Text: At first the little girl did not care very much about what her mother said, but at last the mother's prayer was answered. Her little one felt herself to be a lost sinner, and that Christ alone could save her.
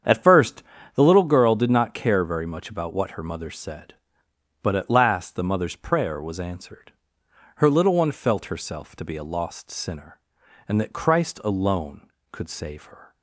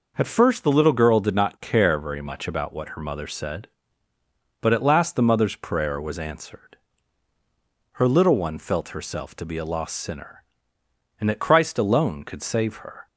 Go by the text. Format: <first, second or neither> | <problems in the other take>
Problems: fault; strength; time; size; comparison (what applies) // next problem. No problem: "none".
second | starts louder than the rest; strong; until 1.3 s; 8 dB // pauses between "first" and "the"; slight; at 0.6 s; 0.32 s long